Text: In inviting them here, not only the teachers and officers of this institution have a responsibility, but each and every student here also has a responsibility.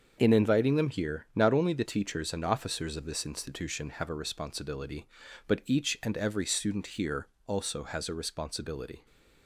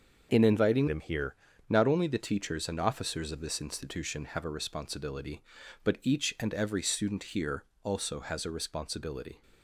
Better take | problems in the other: first | starts louder than the rest; until 1.3 s; 6.5 dB; also in the first // changes voice from "them" to "here"; from 0.8 to 1.3 s; 0.5 s long // pauses between "here" and "also"; slight; at 7.6 s; 0.20 s long; slight in the first

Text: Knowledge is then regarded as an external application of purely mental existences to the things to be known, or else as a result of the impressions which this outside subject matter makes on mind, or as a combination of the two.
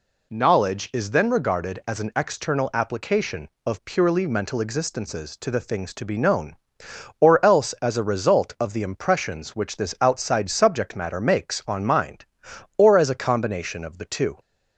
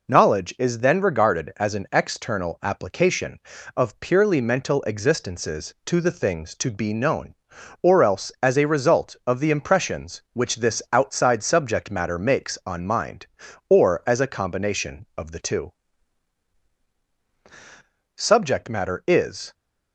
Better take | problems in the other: first | goes on to say "Subject matter is"; from 18.1 s on; 1.3 s long

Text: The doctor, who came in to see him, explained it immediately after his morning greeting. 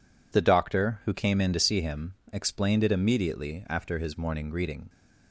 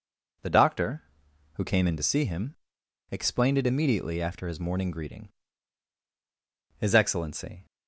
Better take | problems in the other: first | goes on to say "His Excellency"; noticeable; from 6.7 s on; 0.88 s long

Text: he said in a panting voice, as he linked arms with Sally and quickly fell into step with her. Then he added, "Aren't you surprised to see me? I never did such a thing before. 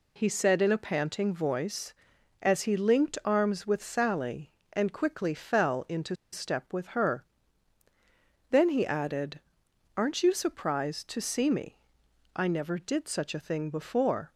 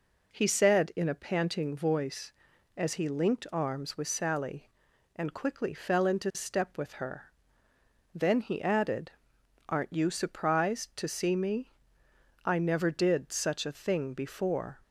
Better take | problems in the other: second | pauses between "into" and "step"; slight; at 6.1 s; 0.17 s long

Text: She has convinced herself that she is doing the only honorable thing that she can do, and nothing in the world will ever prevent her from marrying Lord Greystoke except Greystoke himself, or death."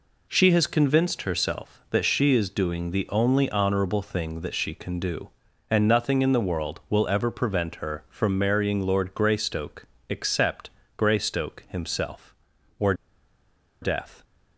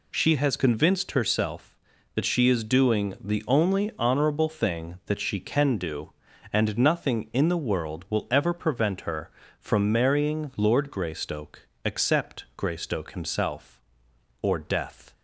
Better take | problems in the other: second | pauses between "Greystoke" and "except"; slight; at 9.8 s; 0.20 s long; slight in the second // pauses between "except" and "Greystoke"; slight; at 10.6 s; 0.28 s long // pauses between "or" and "death"; noticeable; at 12.9 s; 0.88 s long

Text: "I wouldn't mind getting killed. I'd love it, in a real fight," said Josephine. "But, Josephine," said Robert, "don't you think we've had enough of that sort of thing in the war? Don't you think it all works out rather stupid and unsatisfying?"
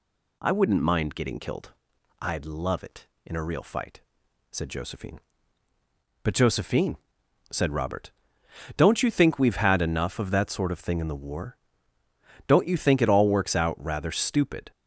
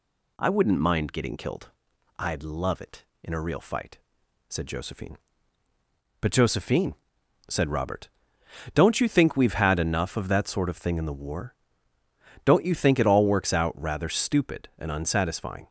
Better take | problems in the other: second | stops before "and unsatisfying"; at 14.7 s

